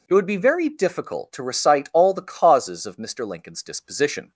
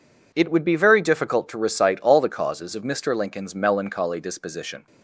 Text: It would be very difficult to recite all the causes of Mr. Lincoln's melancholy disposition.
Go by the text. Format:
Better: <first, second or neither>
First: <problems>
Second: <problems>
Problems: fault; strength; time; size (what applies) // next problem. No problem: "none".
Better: second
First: skips "melancholy"; at 3.6 s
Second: none